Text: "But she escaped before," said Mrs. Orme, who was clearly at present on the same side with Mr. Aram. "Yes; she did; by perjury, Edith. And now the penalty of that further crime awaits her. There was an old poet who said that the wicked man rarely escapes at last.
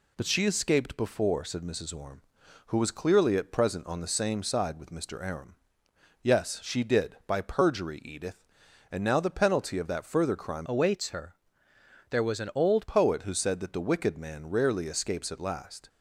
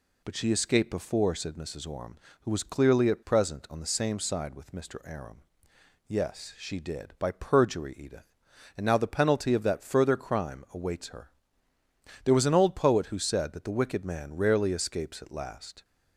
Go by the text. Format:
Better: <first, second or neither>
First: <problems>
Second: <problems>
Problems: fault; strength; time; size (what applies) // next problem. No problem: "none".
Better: second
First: changes voice from "awaits" to "old"; from 10.6 to 12.8 s; 2.2 s long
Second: none